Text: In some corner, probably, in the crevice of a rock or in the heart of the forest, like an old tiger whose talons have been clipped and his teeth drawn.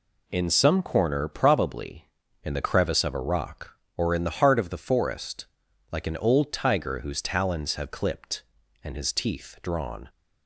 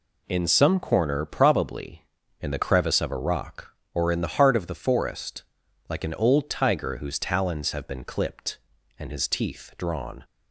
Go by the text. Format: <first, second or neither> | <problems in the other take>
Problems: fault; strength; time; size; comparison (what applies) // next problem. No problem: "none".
second | skips "been"; at 7.9 s